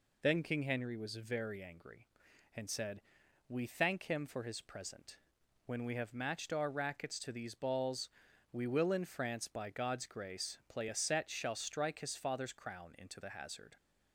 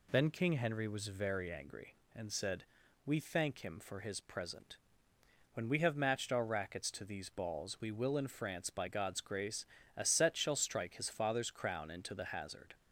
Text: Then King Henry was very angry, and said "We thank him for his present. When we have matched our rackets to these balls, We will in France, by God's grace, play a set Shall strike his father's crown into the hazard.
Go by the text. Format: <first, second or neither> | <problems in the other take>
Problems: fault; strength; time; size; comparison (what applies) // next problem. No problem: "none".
first | pauses between "said" and "We"; at 2.6 s; 0.42 s long; also in the first // skips "play"; at 9.8 s